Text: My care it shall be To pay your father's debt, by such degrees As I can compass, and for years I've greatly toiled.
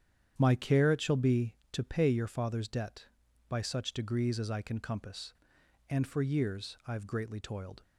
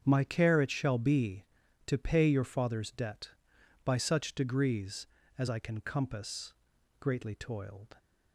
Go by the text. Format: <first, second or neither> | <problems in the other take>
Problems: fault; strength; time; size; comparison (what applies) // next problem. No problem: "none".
first | starts louder than the rest; strong; until 1.0 s; 8 dB; strong in the first // skips "and for years I've"; at 6.7 s